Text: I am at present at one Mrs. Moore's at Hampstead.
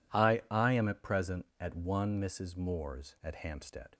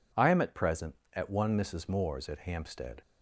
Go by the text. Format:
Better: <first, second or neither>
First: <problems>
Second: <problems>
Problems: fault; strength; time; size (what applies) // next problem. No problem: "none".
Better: second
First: says "I" twice; at 0.5 s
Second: none